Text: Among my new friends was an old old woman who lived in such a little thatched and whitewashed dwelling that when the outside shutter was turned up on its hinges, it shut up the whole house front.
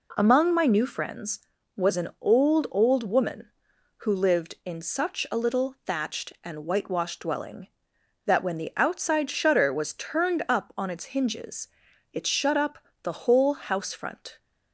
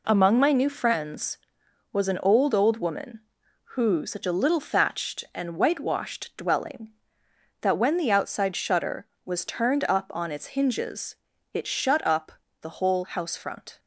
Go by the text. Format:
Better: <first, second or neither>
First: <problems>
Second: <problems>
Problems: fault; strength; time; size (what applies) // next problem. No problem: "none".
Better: first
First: pauses between "up" and "the"; slight; at 12.7 s; 0.24 s long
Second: skips "lived in"; at 4.0 s // pauses between "up" and "the"; slight; at 12.3 s; 0.29 s long